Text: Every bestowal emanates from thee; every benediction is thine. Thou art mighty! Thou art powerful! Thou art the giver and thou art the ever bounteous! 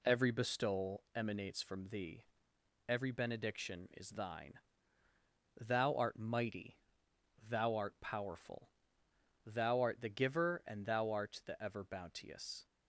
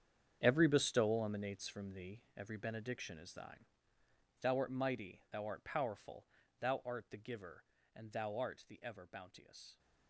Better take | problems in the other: first | gets quieter; strong; throughout; 13.5 dB

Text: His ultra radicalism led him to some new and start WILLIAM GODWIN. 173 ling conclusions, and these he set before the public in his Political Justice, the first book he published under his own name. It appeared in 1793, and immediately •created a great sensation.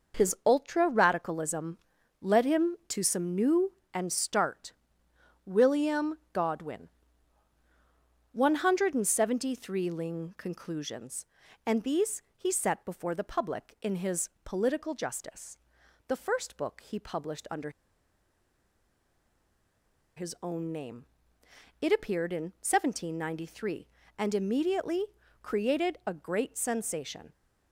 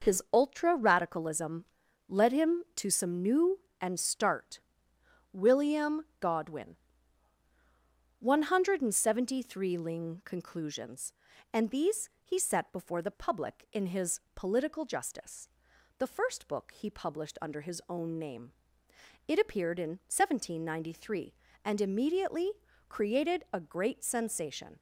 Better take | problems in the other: second | pauses between "radicalism" and "led"; at 1.7 s; 0.44 s long; also in the second // pauses between "start" and "WILLIAM"; noticeable; at 4.7 s; 0.74 s long; noticeable in the second // pauses between "these" and "he"; slight; at 12.2 s; 0.16 s long; slight in the second // pauses between "his" and "Political"; slight; at 14.2 s; 0.16 s long; slight in the second // pauses between "under" and "his"; strong; at 17.7 s; 2.4 s long

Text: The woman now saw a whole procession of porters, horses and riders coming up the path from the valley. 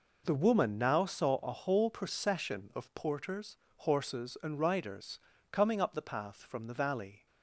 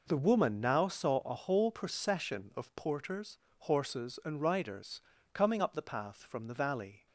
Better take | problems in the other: neither | pauses between "riders" and "coming"; slight; the same in both

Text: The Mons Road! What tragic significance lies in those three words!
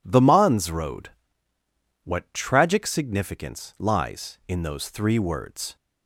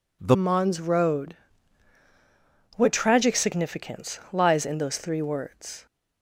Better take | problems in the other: first | changes voice at "Mons"; from 0.3 s on; 5.5 s long

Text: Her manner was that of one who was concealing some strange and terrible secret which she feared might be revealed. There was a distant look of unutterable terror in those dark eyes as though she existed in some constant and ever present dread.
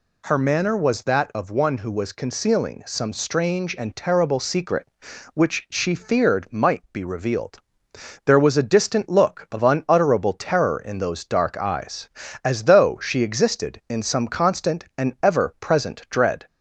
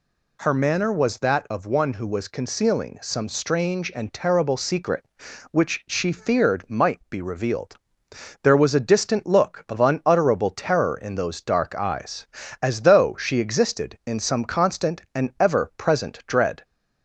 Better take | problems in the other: neither | none

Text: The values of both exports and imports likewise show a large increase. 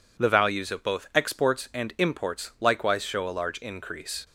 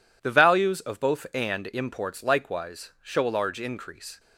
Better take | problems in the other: first | skips "exports"; at 1.2 s

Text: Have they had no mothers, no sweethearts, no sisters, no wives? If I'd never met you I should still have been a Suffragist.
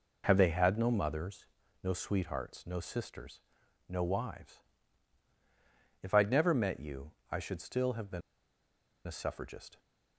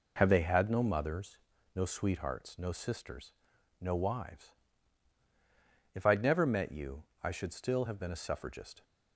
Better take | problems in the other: second | pauses between "you" and "I"; slight; at 7.1 s; 0.20 s long; slight in the second // pauses between "been" and "a"; noticeable; at 8.2 s; 0.86 s long

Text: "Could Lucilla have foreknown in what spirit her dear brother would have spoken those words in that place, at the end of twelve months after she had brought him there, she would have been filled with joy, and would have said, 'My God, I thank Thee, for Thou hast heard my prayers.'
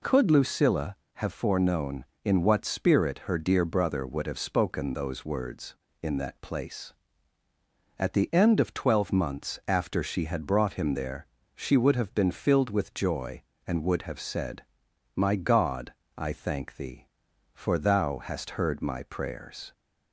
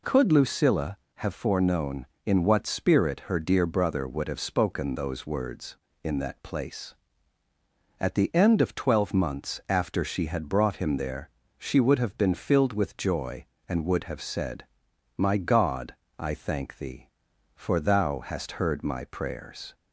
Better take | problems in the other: neither | none

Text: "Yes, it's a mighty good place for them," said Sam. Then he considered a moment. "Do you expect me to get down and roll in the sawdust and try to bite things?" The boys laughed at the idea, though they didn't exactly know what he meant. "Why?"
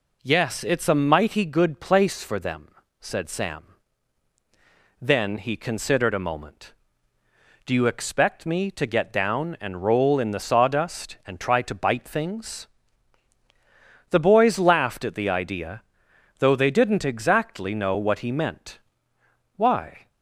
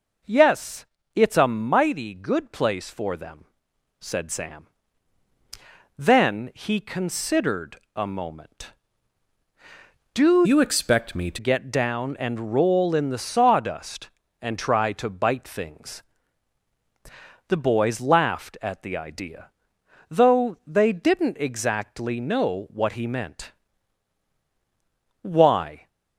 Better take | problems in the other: first | pauses between "considered" and "a"; slight; at 7.7 s; 0.16 s long // changes voice from "you" to "to"; from 10.4 to 11.3 s; 0.9 s long

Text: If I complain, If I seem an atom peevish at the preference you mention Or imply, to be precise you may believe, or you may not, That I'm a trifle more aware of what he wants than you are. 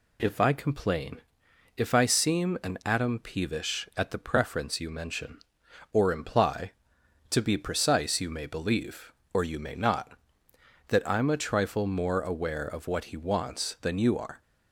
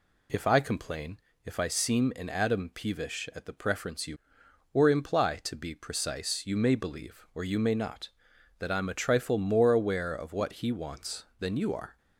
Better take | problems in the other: first | skips "mention"; at 4.4 s

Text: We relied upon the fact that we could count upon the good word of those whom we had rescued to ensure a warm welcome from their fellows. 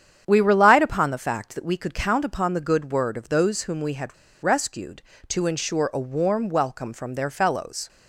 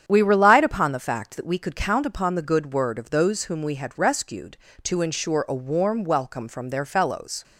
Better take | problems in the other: second | starts louder than the rest; strong; until 1.2 s; 8.5 dB; strong in the second // pauses between "had" and "rescued"; slight; at 4.1 s; 0.27 s long

